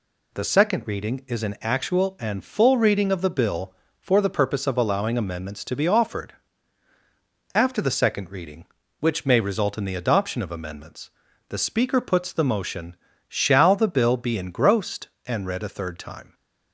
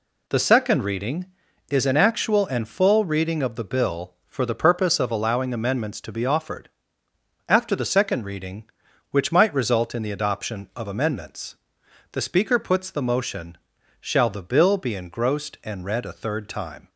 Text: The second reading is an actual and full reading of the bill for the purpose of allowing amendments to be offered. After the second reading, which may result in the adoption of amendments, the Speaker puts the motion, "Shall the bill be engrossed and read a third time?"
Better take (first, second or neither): first